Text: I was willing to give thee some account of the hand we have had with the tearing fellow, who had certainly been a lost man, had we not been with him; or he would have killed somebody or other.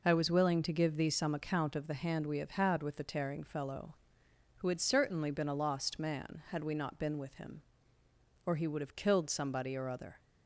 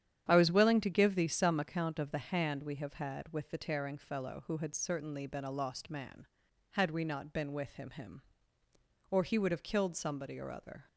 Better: first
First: none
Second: starts louder than the rest; strong; until 1.3 s; 9.5 dB // says "him" twice; at 7.9 s

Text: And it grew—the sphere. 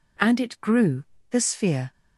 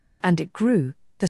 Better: first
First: none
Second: stops before "sphere"; at 1.2 s

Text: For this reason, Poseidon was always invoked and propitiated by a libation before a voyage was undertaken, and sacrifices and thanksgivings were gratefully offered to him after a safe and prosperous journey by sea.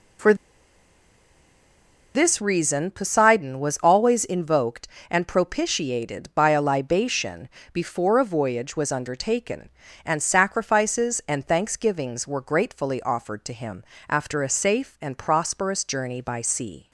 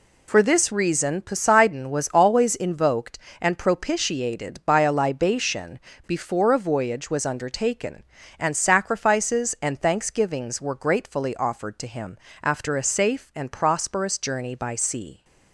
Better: second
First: pauses between "For" and "this"; strong; at 0.3 s; 1.8 s long // pauses between "libation" and "before"; slight; at 7.4 s; 0.24 s long // pauses between "him" and "after"; slight; at 13.8 s; 0.26 s long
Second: pauses between "libation" and "before"; slight; at 5.7 s; 0.28 s long // pauses between "him" and "after"; slight; at 12.1 s; 0.26 s long

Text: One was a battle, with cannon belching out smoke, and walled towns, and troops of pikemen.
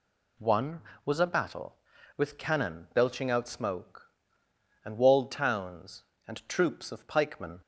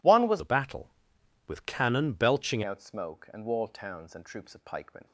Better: first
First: none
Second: changes voice from "a" to "belching"; from 0.3 to 2.6 s; 2.3 s long

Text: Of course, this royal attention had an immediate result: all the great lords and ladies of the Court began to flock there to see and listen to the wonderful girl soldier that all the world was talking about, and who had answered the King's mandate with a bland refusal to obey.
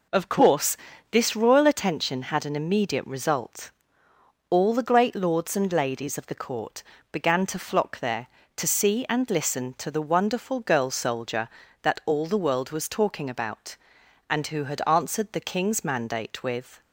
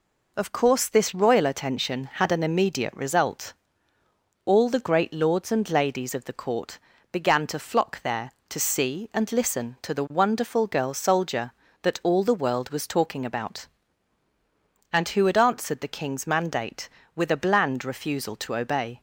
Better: second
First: pauses between "Court" and "began"; slight; at 6.8 s; 0.30 s long // stops before "a bland refusal to obey"; at 16.8 s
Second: pauses between "Court" and "began"; slight; at 6.7 s; 0.32 s long

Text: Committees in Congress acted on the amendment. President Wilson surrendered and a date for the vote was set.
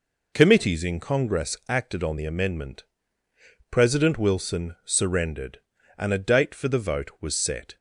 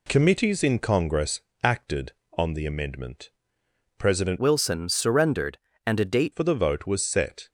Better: first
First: none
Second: pauses between "Congress" and "acted"; slight; at 1.4 s; 0.24 s long // changes voice from "Wilson" to "date"; from 4.3 to 6.3 s; 2.0 s long

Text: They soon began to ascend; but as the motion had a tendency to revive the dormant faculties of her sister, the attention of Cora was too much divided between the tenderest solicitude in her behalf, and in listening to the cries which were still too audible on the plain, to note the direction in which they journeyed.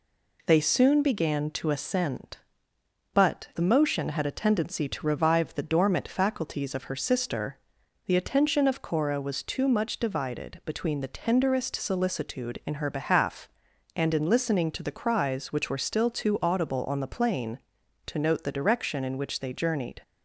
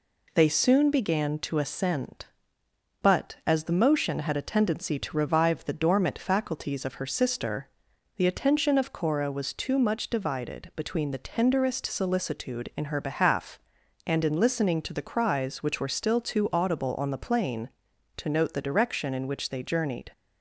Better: second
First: skips "as"; at 3.5 s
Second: none

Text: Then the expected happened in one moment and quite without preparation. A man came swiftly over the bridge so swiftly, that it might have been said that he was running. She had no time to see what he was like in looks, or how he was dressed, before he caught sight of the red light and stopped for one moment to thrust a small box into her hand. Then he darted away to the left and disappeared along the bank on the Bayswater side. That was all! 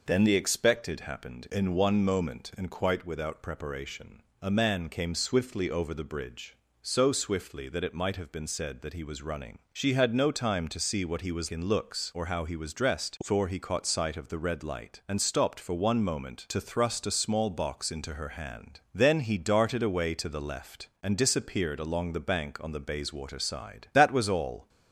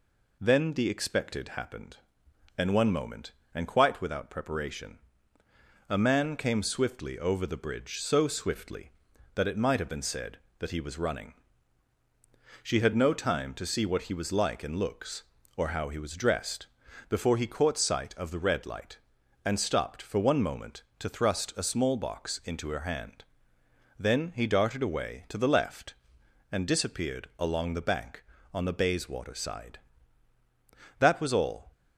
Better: second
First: skips "like"; at 11.4 s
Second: none

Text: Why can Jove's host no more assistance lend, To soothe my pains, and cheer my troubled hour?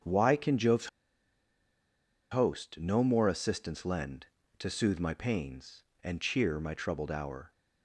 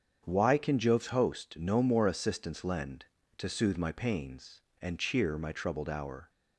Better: second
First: starts louder than the rest; strong; until 2.4 s; 7.5 dB // pauses between "Jove's" and "host"; strong; at 0.8 s; 1.4 s long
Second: starts louder than the rest; strong; until 1.2 s; 7.5 dB

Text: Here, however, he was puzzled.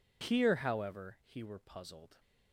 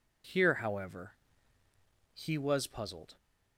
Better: second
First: says "were" for "was"; at 1.4 s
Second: none

